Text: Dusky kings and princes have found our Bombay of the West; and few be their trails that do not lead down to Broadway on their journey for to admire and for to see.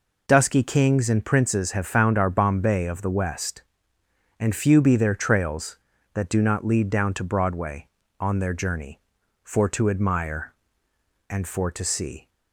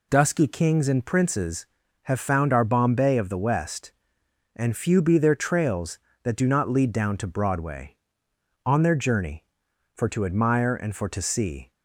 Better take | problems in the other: neither | none

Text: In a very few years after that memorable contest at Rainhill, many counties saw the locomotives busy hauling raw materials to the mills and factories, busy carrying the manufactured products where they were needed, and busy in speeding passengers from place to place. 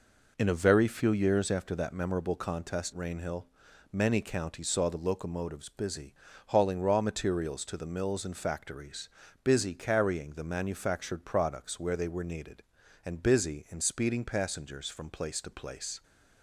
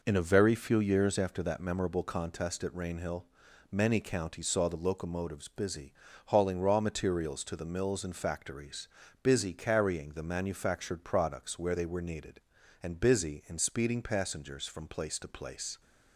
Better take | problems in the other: second | skips "at"; at 2.9 s // pauses between "busy" and "hauling"; slight; at 6.1 s; 0.32 s long; slight in the second

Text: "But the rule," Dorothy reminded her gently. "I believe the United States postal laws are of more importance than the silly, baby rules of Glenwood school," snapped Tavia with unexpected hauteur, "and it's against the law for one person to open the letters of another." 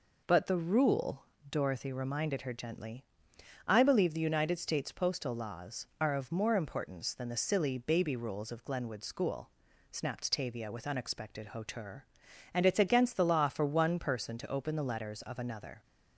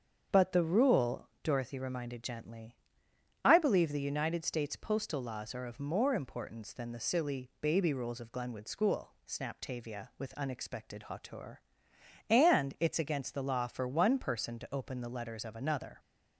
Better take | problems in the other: first | starts louder than the rest; until 1.4 s; 7 dB // skips "her"; at 2.2 s

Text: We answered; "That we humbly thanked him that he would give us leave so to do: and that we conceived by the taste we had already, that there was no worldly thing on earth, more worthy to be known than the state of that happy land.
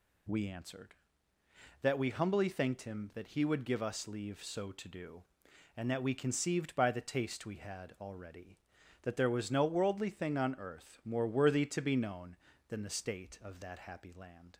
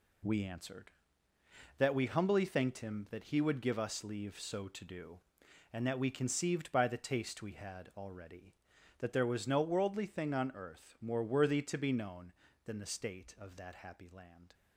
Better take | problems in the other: first | gets quieter; strong; throughout; 8 dB

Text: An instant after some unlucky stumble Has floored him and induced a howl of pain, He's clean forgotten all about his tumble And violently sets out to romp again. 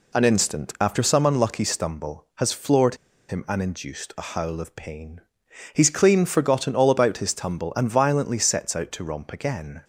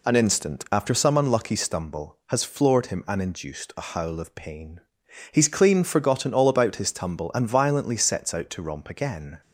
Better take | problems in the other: second | pauses between "floored" and "him"; slight; at 2.9 s; 0.32 s long

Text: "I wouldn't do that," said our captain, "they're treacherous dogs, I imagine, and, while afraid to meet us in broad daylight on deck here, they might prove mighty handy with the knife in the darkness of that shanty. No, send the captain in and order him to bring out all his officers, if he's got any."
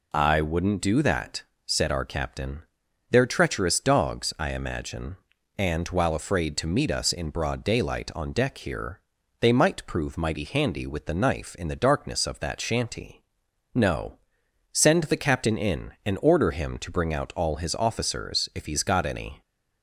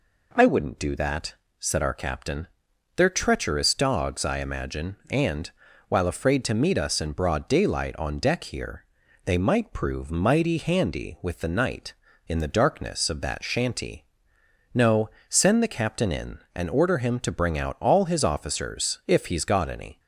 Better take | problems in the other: first | says "night" for "knife"; at 11.4 s

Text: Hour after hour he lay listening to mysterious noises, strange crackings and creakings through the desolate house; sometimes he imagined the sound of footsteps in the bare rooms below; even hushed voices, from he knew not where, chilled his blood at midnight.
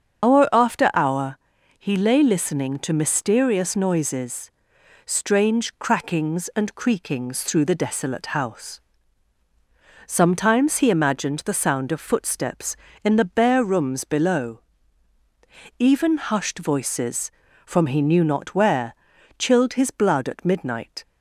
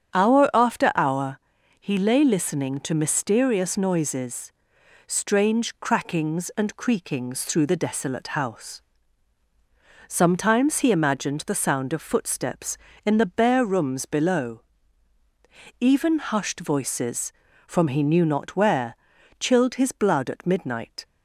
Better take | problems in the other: second | loses the start of "Hour"; at 0.2 s; 110 ms // starts louder than the rest; until 1.3 s; 7 dB; strong in the second // pauses between "hour" and "he"; at 1.3 s; 0.40 s long; also in the second

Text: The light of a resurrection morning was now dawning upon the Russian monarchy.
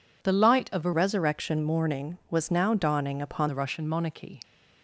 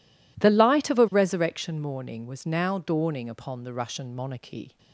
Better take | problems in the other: second | changes voice from "resurrection" to "upon"; from 0.9 to 3.4 s; 2.5 s long

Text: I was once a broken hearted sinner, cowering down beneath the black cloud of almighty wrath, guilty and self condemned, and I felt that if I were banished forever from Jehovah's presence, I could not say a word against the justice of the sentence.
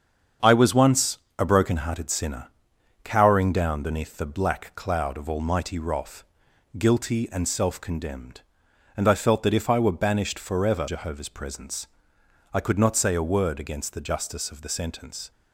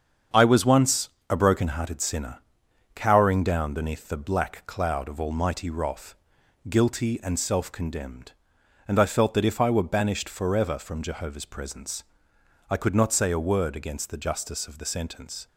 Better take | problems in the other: second | starts louder than the rest; strong; until 1.6 s; 7.5 dB; strong in the second // pauses between "once" and "a"; slight; at 1.1 s; 0.18 s long; slight in the second // skips "from"; at 10.8 s

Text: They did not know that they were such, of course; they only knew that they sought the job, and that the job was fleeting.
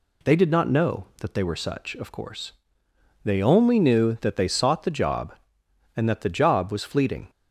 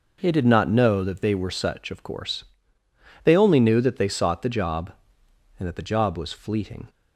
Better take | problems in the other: neither | none

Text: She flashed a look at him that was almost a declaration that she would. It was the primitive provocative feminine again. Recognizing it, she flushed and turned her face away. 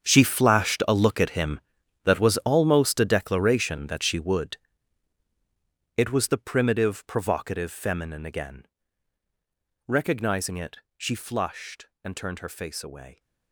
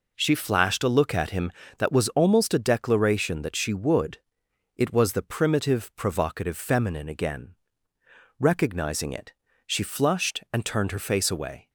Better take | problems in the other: second | gets quieter; strong; throughout; 15 dB

